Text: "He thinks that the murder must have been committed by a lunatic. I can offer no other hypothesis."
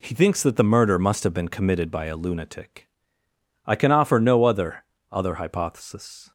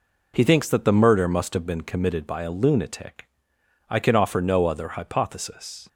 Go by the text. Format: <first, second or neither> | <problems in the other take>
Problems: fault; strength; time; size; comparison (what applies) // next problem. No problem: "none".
second | says "other" twice; at 5.1 s